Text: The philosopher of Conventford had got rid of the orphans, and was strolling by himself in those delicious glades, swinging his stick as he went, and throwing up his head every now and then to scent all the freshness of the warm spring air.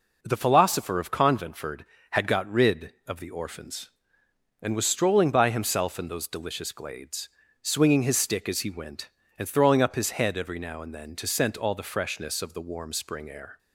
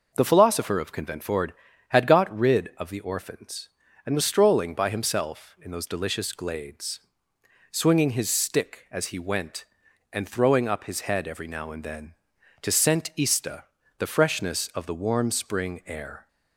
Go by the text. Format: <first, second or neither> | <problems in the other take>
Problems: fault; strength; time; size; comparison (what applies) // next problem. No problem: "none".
first | says "ista" for "all"; at 13.1 s